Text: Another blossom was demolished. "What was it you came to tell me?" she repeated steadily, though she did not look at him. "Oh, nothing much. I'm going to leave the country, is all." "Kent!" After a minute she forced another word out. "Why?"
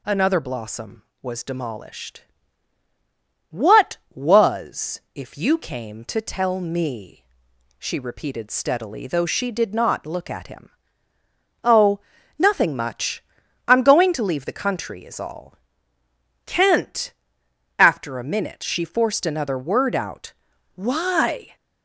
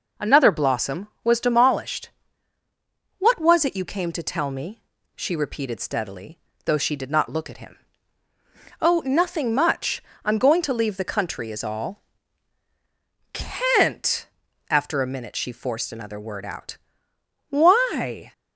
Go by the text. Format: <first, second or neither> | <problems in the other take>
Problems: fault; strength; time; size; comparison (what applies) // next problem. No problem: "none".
second | says "if" for "it"; at 5.1 s